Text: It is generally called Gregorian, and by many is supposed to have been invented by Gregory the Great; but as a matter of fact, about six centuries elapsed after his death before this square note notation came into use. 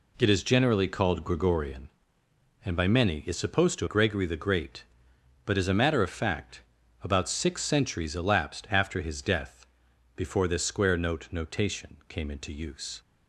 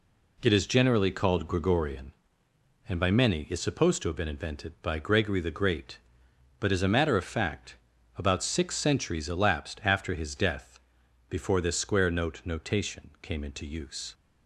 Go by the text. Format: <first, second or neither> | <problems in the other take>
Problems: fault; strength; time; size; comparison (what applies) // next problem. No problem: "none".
second | skips "have been invented by"; at 3.8 s // pauses between "death" and "before"; noticeable; at 9.6 s; 0.50 s long; noticeable in the second